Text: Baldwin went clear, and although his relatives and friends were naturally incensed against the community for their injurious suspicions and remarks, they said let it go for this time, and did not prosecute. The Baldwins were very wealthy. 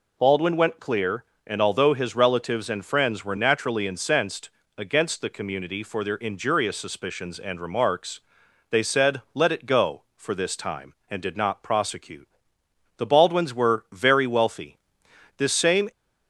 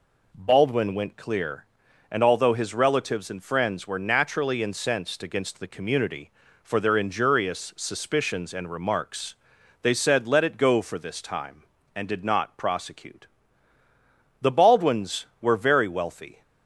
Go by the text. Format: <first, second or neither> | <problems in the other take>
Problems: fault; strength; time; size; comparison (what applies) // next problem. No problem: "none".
second | pauses between "incensed" and "against"; slight; at 4.4 s; 0.30 s long // goes on to say "This same"; from 15.3 s on; 0.54 s long